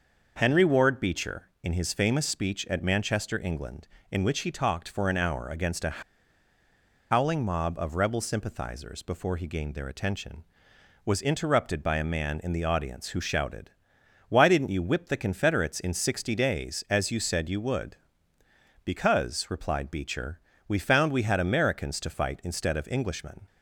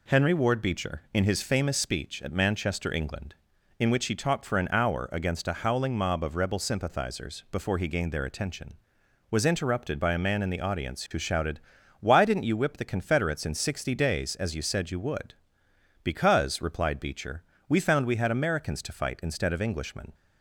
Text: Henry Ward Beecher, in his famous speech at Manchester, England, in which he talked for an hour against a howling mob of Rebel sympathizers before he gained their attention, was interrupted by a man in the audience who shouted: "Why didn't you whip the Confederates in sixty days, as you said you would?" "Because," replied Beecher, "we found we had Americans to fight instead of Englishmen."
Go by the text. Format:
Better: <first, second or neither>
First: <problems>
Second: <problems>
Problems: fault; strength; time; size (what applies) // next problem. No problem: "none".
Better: second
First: starts louder than the rest; noticeable; until 1.3 s; 6 dB // pauses between "a" and "howling"; at 6.0 s; 1.1 s long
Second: none